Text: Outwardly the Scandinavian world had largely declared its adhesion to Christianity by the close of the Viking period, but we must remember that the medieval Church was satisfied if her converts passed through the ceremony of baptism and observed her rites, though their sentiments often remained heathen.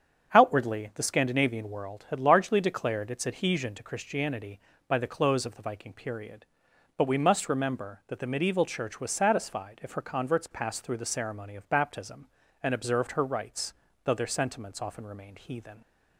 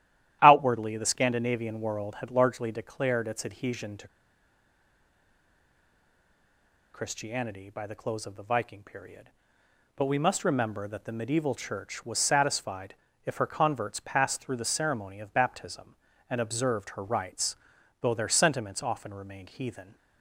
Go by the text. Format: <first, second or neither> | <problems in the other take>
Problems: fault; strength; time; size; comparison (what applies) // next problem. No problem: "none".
first | starts louder than the rest; strong; until 1.4 s; 12.5 dB; strong in the first // pauses between "to" and "Christianity"; strong; at 4.0 s; 2.8 s long // pauses between "satisfied" and "if"; slight; at 12.9 s; 0.30 s long